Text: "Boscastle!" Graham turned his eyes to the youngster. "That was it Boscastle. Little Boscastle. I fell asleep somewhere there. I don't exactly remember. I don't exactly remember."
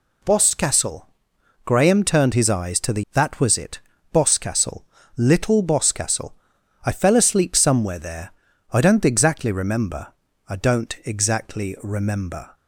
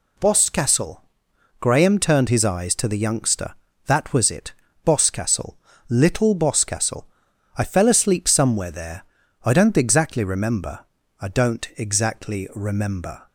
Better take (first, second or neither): second